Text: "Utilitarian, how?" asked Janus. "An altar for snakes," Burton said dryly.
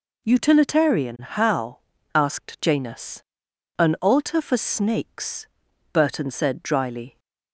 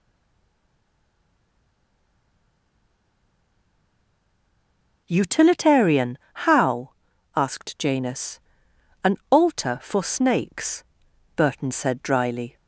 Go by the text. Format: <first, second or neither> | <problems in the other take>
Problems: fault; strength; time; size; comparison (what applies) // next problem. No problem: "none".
first | stays silent before the first word; strong; until 5.0 s; 5.0 s long